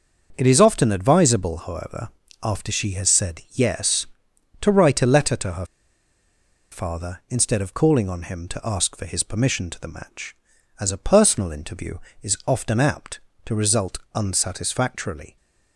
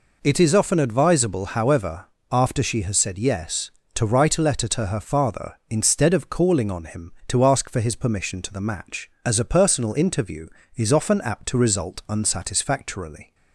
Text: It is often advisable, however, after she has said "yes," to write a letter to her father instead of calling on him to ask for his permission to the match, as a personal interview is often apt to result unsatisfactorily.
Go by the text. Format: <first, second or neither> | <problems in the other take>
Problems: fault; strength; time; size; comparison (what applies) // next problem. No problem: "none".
second | starts louder than the rest; until 1.3 s; 6.5 dB // pauses between "her" and "father"; at 5.6 s; 1.0 s long // pauses between "result" and "unsatisfactorily"; slight; at 13.9 s; 0.16 s long